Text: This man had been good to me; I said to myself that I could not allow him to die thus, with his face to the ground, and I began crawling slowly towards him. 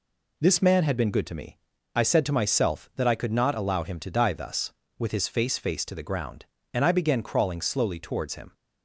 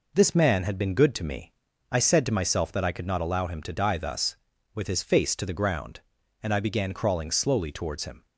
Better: second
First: says "face" twice; at 5.5 s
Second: none

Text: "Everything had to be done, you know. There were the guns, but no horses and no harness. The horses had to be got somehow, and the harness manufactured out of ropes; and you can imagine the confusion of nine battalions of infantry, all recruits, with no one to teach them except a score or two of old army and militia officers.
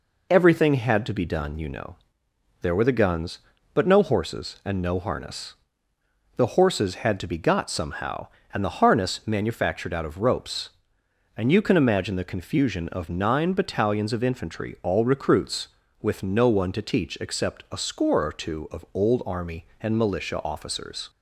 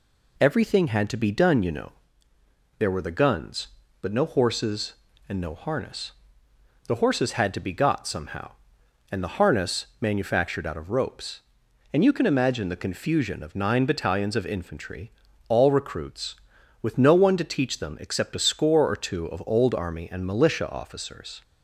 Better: second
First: skips "them"; at 17.1 s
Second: none

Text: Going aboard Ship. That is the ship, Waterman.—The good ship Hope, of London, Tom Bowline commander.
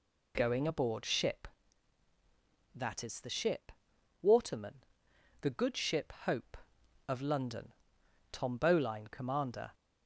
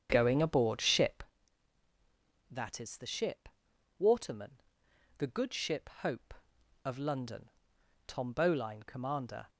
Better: first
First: none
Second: starts louder than the rest; strong; until 1.2 s; 8 dB

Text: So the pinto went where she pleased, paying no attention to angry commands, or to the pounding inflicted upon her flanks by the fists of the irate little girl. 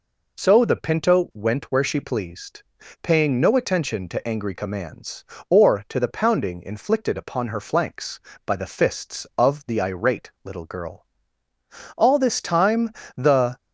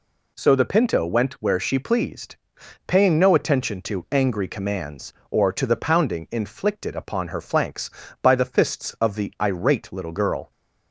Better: second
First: goes on to say "All this time the"; from 11.9 s on; 1.6 s long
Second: none

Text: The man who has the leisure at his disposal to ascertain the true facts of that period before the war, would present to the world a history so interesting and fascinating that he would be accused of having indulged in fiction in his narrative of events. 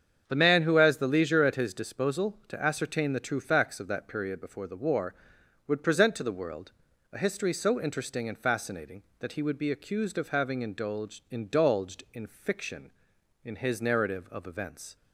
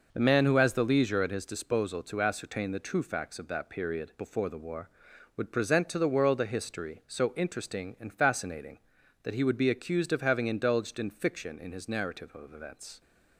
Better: second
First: starts louder than the rest; strong; until 1.2 s; 7.5 dB // pauses between "world" and "a"; at 6.7 s; 0.42 s long // says "indulged" twice; at 11.2 s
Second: none

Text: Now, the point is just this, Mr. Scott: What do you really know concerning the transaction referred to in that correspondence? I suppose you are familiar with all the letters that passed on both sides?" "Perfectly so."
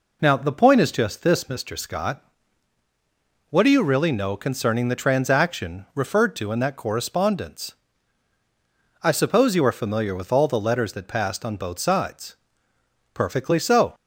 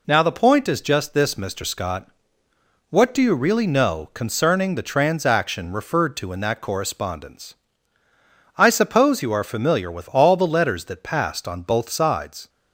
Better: first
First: none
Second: stops before "Perfectly so"; at 12.4 s

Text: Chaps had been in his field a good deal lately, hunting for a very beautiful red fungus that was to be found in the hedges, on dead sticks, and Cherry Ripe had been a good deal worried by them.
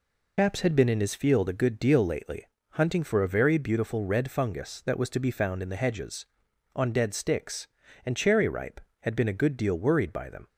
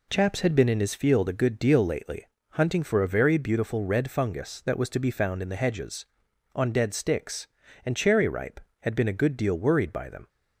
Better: second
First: loses the start of "Chaps"; at 0.3 s; 75 ms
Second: none

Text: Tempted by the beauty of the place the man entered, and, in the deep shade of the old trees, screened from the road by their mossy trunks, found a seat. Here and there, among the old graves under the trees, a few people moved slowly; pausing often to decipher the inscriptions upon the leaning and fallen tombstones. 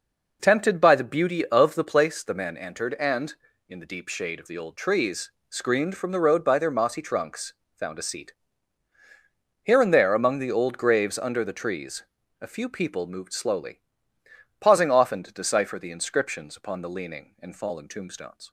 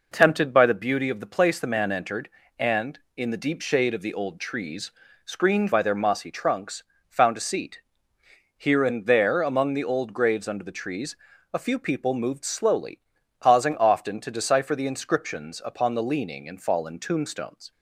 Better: first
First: none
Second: skips "from the road"; at 5.7 s

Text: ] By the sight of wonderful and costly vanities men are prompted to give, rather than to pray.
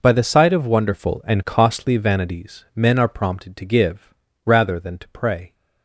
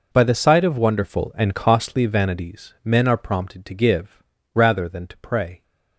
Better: neither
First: none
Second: none

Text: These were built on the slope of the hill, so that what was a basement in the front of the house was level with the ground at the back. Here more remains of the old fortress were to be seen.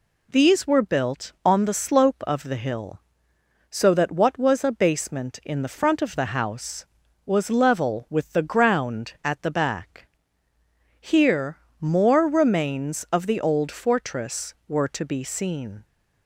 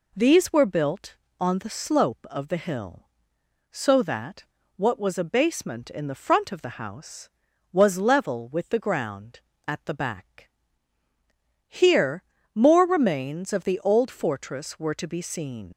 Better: first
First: pauses between "Here" and "more"; slight; at 11.5 s; 0.24 s long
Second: pauses between "that" and "what"; slight; at 4.4 s; 0.34 s long // pauses between "Here" and "more"; slight; at 12.2 s; 0.32 s long // leaves "seen" unfinished; at 15.7 s; 80 ms

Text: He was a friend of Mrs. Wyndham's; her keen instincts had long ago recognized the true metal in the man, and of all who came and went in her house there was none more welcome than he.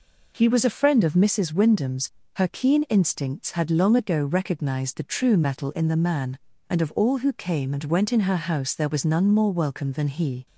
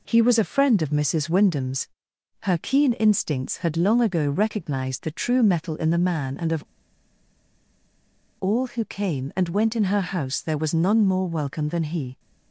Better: first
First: none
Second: pauses between "of" and "all"; strong; at 6.6 s; 1.7 s long

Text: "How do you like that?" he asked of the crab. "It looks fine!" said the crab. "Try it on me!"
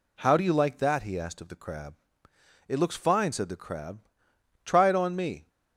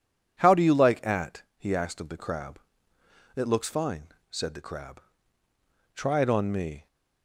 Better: first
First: none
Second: says "at" for "that"; at 1.0 s

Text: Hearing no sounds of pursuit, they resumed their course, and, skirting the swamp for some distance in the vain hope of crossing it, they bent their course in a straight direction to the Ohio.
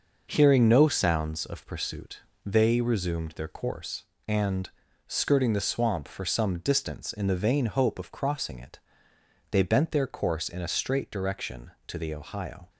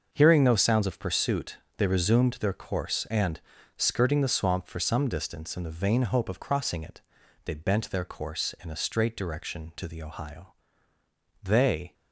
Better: first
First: none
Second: starts louder than the rest; until 1.1 s; 6 dB // goes on to say "They"; from 11.4 s on; 0.50 s long

